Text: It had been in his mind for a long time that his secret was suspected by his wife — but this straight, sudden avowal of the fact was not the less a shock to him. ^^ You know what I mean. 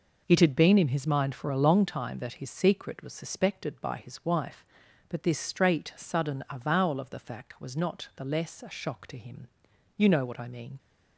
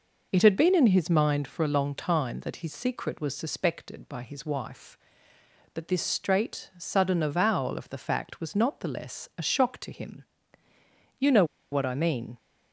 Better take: first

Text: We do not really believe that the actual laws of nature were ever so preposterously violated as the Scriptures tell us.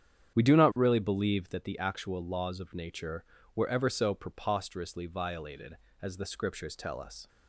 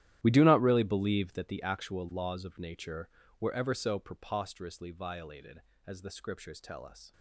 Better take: first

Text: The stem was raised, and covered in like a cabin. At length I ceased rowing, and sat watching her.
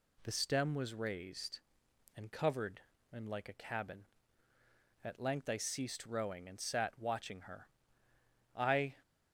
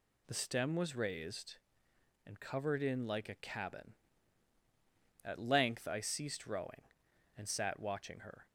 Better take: second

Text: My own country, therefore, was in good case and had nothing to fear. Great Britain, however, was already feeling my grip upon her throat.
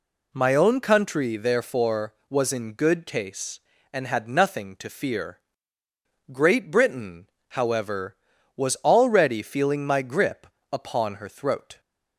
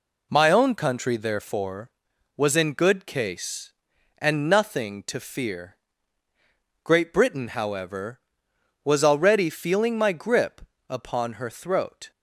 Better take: first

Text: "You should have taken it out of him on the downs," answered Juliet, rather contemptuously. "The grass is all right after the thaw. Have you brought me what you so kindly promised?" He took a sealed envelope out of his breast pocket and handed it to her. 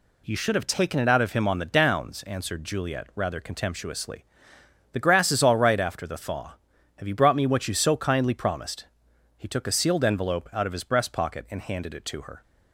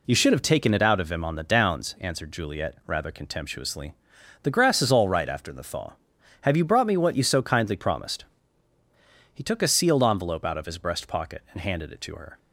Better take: neither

